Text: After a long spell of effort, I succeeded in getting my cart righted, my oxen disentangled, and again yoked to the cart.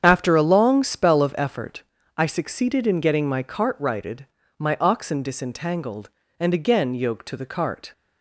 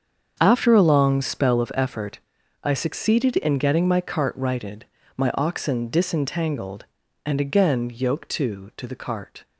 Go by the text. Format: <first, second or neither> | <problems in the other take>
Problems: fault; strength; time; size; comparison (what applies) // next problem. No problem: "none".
first | starts louder than the rest; strong; until 1.4 s; 7 dB; strong in the first // says "to" twice; at 8.7 s